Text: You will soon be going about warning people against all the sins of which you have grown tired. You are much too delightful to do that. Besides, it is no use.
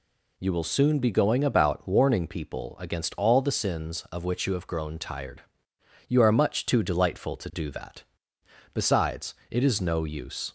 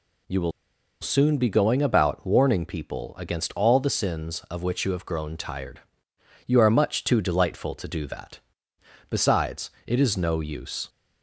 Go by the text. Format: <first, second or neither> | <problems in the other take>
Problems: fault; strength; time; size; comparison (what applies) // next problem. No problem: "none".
first | pauses between "will" and "soon"; noticeable; at 0.5 s; 0.51 s long